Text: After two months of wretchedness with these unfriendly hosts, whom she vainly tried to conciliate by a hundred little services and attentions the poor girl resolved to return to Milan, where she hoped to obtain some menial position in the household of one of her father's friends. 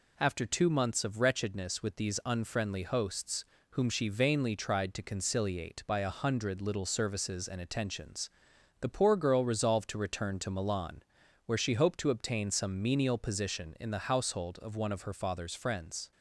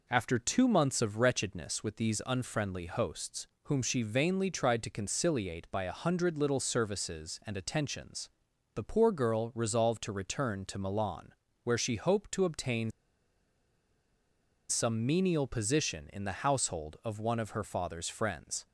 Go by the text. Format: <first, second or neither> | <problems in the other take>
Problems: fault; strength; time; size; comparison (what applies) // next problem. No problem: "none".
first | pauses between "attentions" and "the"; noticeable; at 8.2 s; 0.46 s long; noticeable in the first // pauses between "obtain" and "some"; strong; at 12.9 s; 1.7 s long